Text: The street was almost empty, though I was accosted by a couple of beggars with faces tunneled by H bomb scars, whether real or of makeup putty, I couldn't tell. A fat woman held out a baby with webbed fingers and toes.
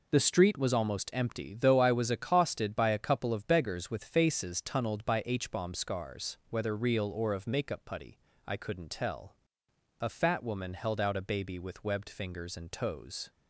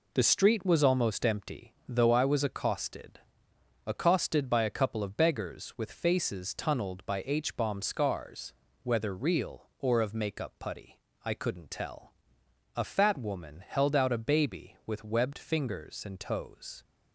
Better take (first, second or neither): first